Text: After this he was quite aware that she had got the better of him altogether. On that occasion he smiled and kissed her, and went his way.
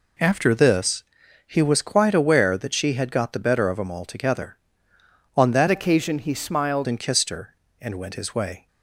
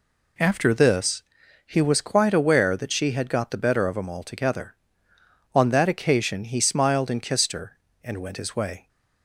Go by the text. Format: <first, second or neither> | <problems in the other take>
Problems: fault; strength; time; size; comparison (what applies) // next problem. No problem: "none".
second | pauses between "this" and "he"; noticeable; at 1.0 s; 0.46 s long; noticeable in the second // changes voice from "occasion" to "smiled"; from 5.6 to 6.8 s; 1.2 s long